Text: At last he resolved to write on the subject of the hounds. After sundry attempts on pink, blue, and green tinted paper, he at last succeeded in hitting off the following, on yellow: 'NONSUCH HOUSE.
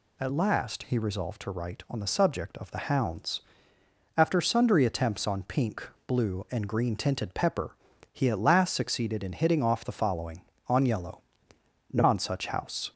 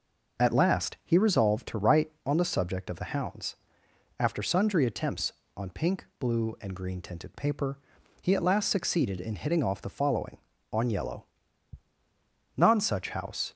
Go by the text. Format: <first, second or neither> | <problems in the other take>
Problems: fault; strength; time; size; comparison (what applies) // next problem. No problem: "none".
second | says "pepper" for "paper"; at 7.3 s